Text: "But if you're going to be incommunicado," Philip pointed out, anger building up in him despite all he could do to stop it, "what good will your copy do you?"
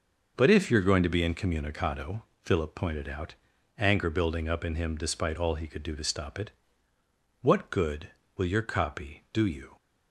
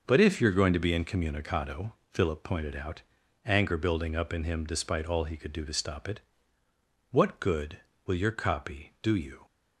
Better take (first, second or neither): neither